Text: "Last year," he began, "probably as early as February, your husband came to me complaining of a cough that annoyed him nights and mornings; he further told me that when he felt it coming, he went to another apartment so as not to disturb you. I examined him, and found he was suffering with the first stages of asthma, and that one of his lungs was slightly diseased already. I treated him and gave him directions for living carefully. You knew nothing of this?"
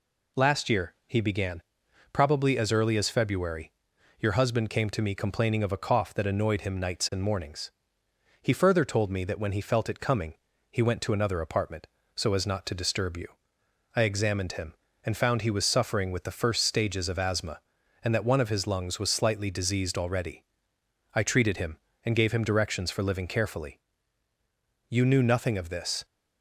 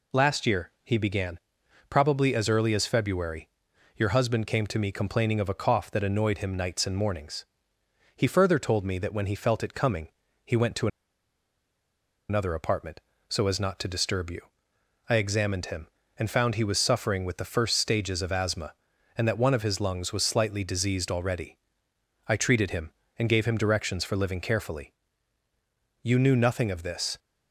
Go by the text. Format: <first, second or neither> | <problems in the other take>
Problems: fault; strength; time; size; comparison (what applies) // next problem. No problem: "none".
first | pauses between "to" and "another"; strong; at 10.8 s; 1.4 s long